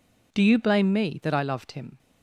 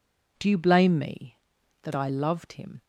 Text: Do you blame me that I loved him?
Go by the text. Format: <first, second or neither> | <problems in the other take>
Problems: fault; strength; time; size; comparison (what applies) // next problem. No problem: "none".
neither | none